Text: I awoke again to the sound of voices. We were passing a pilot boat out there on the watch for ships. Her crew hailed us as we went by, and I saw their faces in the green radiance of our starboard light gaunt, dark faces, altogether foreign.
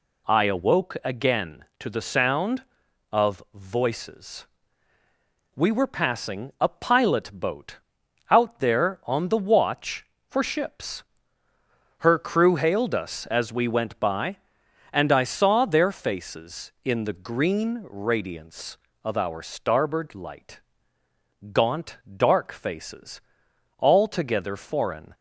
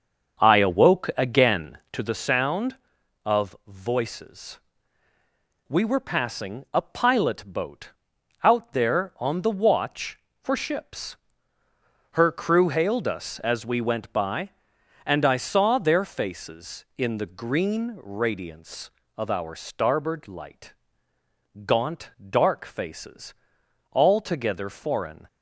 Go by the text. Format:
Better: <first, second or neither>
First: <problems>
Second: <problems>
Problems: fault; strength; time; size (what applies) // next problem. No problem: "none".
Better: first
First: pauses between "boat" and "out"; noticeable; at 7.7 s; 0.52 s long // pauses between "light" and "gaunt"; noticeable; at 20.6 s; 0.90 s long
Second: starts louder than the rest; until 2.3 s; 7 dB // pauses between "boat" and "out"; noticeable; at 7.9 s; 0.52 s long // pauses between "light" and "gaunt"; noticeable; at 20.7 s; 0.90 s long